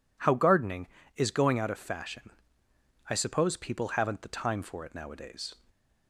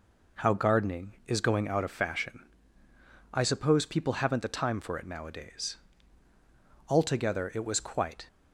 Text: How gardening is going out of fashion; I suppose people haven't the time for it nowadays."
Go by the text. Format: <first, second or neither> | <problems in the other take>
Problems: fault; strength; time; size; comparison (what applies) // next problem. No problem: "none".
first | goes on to say "Altogether it was quite"; from 6.8 s on; 1.3 s long